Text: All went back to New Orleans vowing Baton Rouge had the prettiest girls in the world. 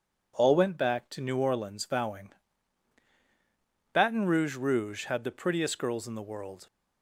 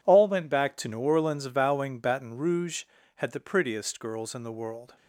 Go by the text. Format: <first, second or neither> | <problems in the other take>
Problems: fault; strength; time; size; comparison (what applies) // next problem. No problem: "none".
second | pauses between "vowing" and "Baton"; strong; at 2.3 s; 1.6 s long // says "Rouge" twice; at 4.5 s